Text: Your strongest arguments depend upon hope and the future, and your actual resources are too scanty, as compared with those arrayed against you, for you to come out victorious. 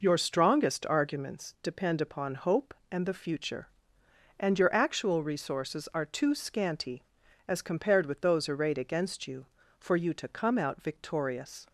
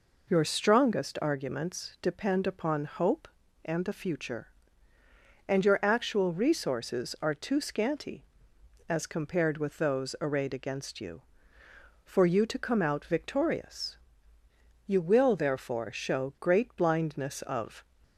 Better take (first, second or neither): first